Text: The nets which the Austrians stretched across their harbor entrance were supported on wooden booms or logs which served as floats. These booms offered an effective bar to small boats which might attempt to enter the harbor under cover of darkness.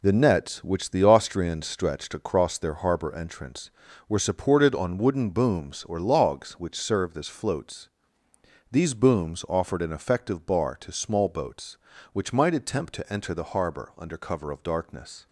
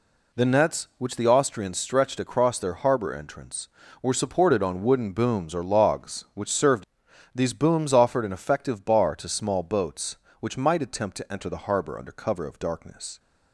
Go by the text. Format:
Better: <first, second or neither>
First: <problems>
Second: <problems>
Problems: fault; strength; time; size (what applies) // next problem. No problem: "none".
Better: first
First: none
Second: skips "as floats"; at 7.0 s